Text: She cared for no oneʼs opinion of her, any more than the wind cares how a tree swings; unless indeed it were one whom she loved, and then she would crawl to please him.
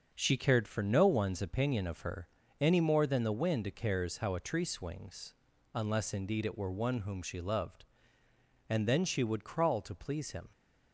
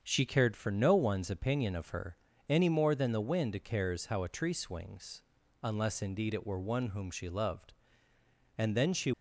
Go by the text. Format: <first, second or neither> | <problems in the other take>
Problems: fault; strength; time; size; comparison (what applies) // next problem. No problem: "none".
first | starts louder than the rest; until 1.0 s; 7 dB; noticeable in the first // stops before "would crawl to please him"; at 9.1 s